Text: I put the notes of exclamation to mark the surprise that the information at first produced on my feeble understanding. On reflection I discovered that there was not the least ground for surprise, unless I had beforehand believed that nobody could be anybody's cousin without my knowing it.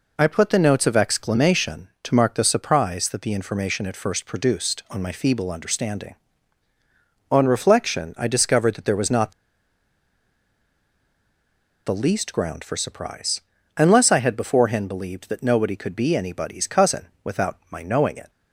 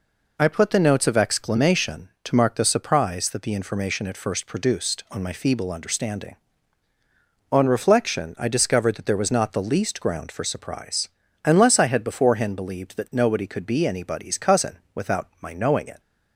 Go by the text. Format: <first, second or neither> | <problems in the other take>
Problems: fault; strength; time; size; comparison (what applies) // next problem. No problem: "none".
second | pauses between "not" and "the"; strong; at 9.3 s; 2.5 s long // pauses between "cousin" and "without"; slight; at 17.0 s; 0.18 s long; slight in the second